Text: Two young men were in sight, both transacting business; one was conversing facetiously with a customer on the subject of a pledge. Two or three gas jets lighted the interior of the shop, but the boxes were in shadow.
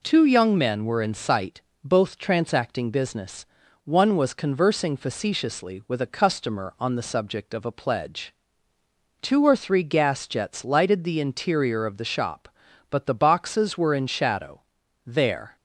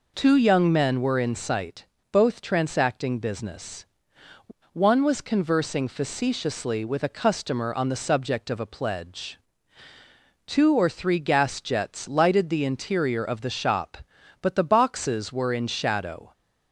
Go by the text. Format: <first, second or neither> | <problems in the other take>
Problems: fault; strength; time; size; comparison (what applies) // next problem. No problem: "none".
second | goes on to say "There"; from 15.0 s on; 0.50 s long